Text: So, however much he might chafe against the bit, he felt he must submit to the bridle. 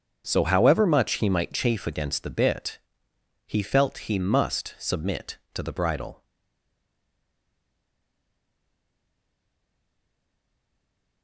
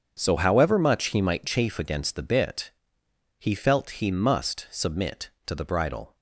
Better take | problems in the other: second | starts louder than the rest; strong; until 1.2 s; 7 dB; strong in the second // stays silent after the last word; strong; from 6.2 s on; 5.0 s long

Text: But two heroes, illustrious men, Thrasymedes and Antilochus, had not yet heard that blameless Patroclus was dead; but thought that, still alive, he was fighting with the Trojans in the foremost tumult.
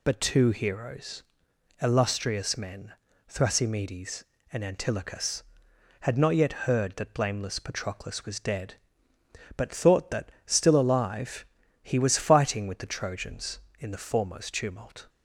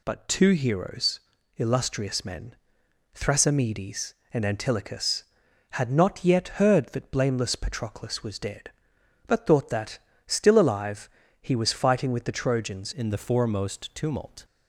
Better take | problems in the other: first | changes voice at "in"; from 12.9 s on; 1.5 s long

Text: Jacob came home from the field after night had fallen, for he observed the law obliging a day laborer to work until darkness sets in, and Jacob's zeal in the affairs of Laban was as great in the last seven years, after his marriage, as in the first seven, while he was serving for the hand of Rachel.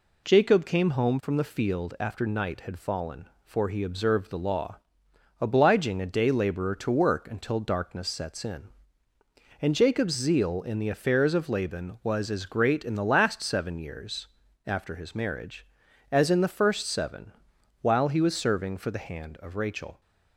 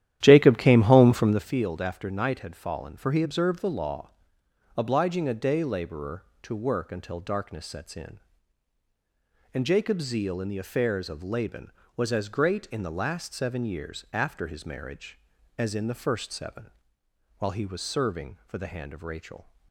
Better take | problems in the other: first | starts louder than the rest; strong; until 1.5 s; 12 dB // pauses between "law" and "obliging"; noticeable; at 4.0 s; 0.68 s long; noticeable in the first

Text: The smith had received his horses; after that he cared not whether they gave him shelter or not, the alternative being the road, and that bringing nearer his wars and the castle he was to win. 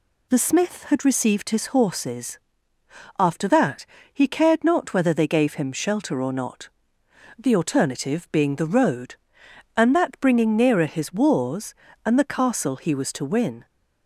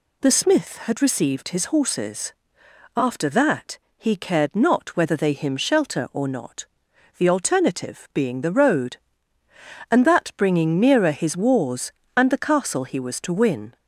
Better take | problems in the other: first | pauses between "that" and "he"; slight; at 3.7 s; 0.18 s long; slight in the first // skips "gave"; at 5.3 s

